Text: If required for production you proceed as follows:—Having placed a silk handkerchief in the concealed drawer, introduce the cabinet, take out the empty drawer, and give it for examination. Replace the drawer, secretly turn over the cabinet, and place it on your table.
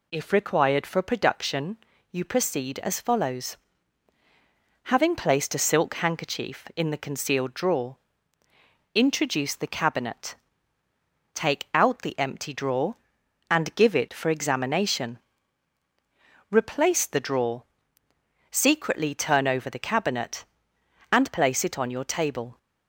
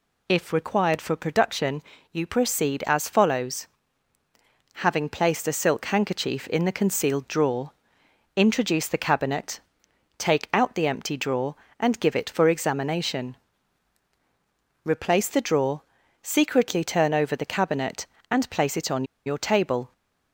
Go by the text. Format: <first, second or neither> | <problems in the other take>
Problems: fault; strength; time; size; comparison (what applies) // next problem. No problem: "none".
first | pauses between "production" and "you"; slight; at 1.8 s; 0.30 s long; slight in the first // pauses between "on" and "your"; slight; at 19.0 s; 0.21 s long